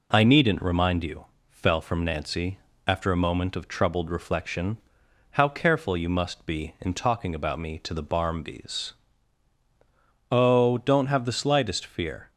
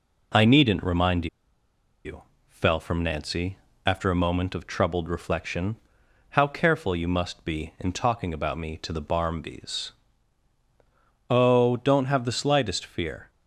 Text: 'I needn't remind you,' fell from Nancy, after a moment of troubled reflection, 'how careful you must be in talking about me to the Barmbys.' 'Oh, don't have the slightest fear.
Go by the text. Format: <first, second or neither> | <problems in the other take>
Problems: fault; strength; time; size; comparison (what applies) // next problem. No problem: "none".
first | pauses between "remind" and "you"; noticeable; at 1.2 s; 0.78 s long